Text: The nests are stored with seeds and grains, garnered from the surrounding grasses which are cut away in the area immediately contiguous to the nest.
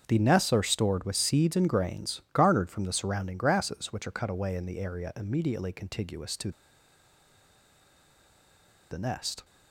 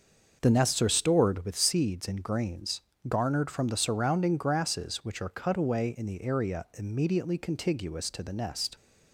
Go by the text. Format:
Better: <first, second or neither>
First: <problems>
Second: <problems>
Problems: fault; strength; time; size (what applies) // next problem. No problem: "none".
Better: second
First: starts louder than the rest; strong; until 1.0 s; 7 dB // pauses between "to" and "the"; strong; at 6.5 s; 2.3 s long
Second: starts louder than the rest; until 1.4 s; 6 dB